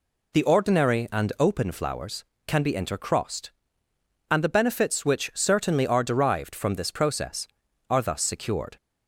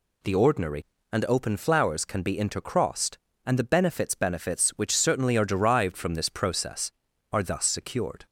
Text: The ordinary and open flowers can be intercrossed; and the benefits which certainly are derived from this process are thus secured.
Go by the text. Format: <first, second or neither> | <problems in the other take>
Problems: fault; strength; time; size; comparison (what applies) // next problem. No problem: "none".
first | says "benefits" twice; at 4.1 s